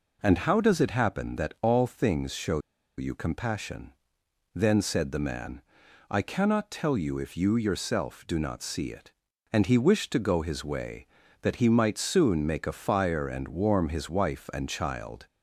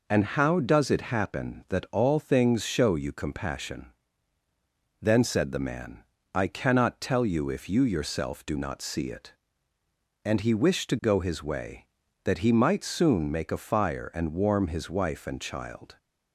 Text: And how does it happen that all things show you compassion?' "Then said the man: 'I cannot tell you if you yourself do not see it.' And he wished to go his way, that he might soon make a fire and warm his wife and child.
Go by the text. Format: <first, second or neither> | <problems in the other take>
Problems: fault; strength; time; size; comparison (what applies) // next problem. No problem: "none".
second | pauses between "show" and "you"; at 2.5 s; 0.38 s long